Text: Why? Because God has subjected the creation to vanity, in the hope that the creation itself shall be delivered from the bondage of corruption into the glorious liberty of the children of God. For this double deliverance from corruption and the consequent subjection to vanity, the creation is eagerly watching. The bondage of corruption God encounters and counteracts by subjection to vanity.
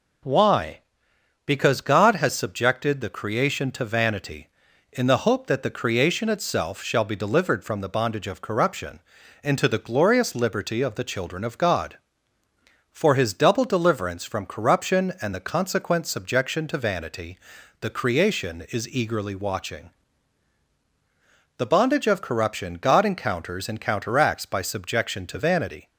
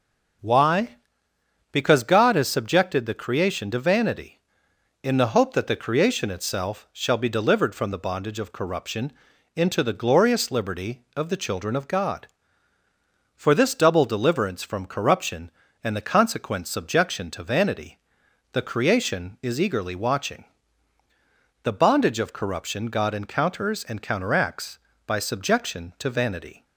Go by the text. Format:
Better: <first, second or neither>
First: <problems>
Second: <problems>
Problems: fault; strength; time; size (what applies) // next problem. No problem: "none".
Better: second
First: pauses between "corruption" and "into"; at 8.9 s; 0.42 s long // says "his" for "this"; at 13.1 s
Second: pauses between "corruption" and "into"; at 9.1 s; 0.42 s long